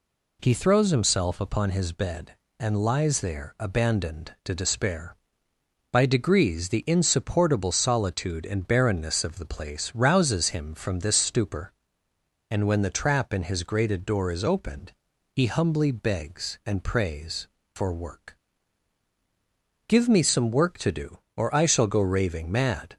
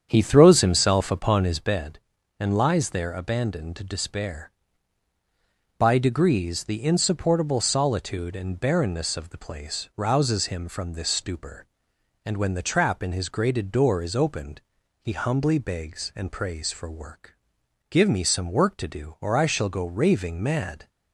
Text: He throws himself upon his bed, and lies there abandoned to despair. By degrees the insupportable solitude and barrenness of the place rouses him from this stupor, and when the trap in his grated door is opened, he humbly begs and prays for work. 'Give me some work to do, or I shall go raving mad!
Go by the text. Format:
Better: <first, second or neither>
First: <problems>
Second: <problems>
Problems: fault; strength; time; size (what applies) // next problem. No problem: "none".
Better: first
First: none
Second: starts louder than the rest; strong; until 1.8 s; 8.5 dB